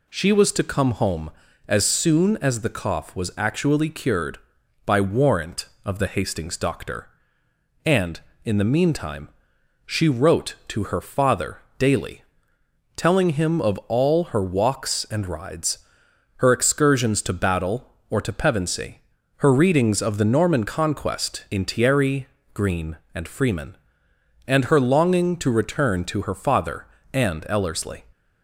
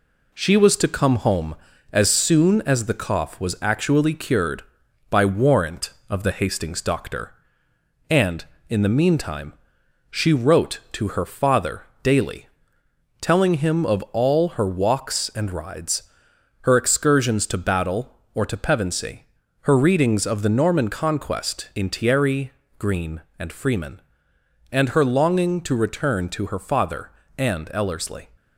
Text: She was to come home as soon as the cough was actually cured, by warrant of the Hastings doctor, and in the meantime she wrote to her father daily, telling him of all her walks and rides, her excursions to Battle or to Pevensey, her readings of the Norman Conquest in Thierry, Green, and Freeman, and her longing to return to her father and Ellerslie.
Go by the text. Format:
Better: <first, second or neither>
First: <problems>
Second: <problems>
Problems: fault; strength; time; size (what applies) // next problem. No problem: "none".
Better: first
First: pauses between "meantime" and "she"; noticeable; at 9.2 s; 0.58 s long // pauses between "father" and "daily"; slight; at 11.5 s; 0.18 s long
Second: gets quieter; throughout; 4 dB // pauses between "meantime" and "she"; noticeable; at 9.5 s; 0.58 s long // pauses between "father" and "daily"; slight; at 11.8 s; 0.18 s long